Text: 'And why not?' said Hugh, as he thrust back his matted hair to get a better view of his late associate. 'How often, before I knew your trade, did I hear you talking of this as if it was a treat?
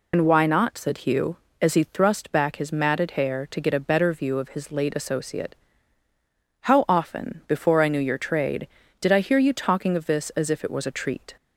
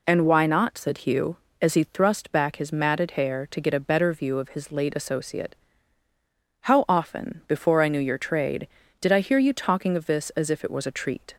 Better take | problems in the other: second | loses the start of "And"; at 0.1 s; 75 ms

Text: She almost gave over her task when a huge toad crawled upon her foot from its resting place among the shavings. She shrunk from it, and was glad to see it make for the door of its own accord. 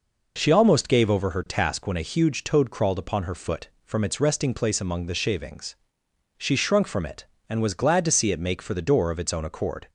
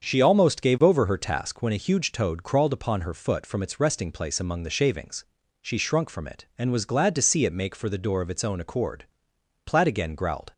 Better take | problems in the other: first | starts louder than the rest; until 1.0 s; 7 dB // goes on to say "Platt again growled"; noticeable; from 9.6 s on; 0.88 s long

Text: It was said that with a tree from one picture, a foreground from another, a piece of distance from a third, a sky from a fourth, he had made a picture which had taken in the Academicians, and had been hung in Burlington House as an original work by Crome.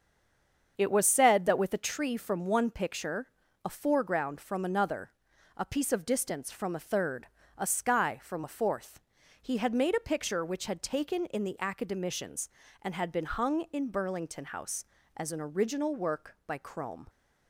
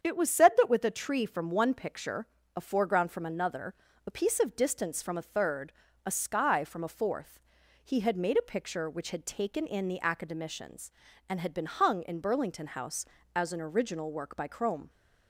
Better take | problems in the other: second | stays silent before the first word; slight; until 0.7 s; 0.7 s long // starts louder than the rest; until 1.7 s; 7 dB; strong in the second

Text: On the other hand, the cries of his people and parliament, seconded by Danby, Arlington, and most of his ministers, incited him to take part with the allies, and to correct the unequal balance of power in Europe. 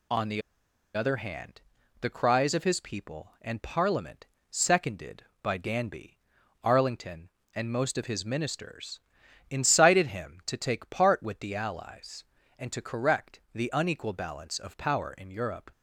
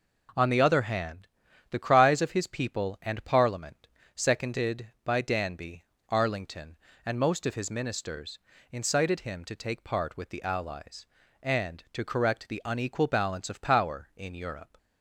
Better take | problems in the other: second | pauses between "the" and "other"; noticeable; at 0.4 s; 0.54 s long

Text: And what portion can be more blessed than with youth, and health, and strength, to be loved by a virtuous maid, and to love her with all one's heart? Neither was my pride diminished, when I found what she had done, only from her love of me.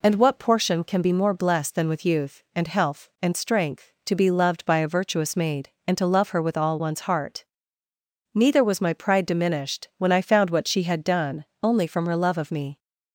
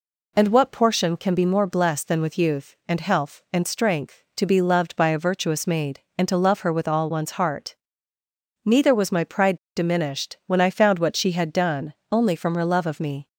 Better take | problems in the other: first | pauses between "pride" and "diminished"; slight; at 9.5 s; 0.19 s long

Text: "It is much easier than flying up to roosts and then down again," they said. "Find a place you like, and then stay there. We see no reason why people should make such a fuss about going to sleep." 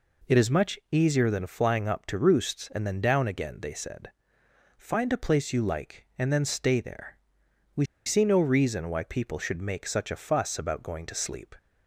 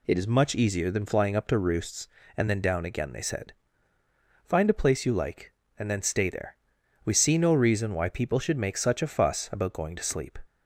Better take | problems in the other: second | pauses between "We" and "see"; slight; at 7.8 s; 0.21 s long

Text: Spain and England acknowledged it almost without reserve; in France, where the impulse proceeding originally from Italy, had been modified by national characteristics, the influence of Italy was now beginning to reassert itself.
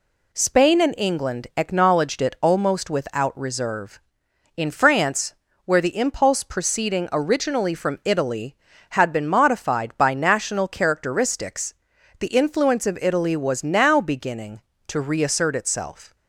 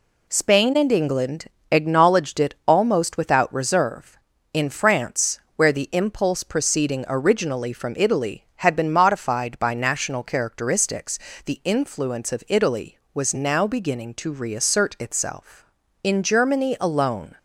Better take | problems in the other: first | pauses between "England" and "acknowledged"; slight; at 1.4 s; 0.26 s long // goes on to say "In Germany alone"; from 16.0 s on; 1.3 s long

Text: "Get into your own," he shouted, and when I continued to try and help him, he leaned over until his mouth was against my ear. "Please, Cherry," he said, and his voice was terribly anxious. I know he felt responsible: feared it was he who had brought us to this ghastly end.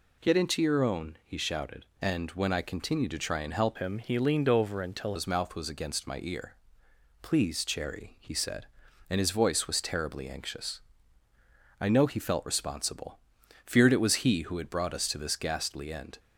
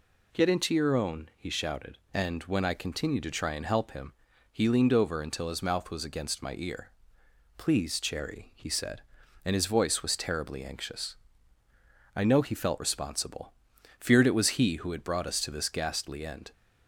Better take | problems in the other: second | changes voice from "him" to "until"; from 3.7 to 5.1 s; 1.4 s long

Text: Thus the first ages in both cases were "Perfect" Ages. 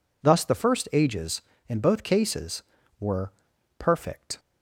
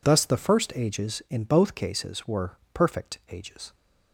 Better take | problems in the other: second | pauses between "were" and "Perfect"; noticeable; at 3.3 s; 0.46 s long; slight in the second // stops before "Ages"; at 4.3 s

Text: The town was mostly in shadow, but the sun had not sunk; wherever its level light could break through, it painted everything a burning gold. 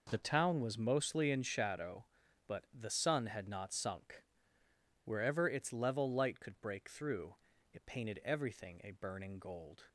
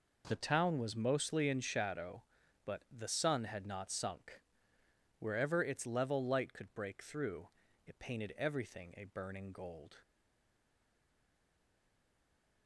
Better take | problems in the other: first | stays silent after the last word; strong; from 10.0 s on; 2.6 s long

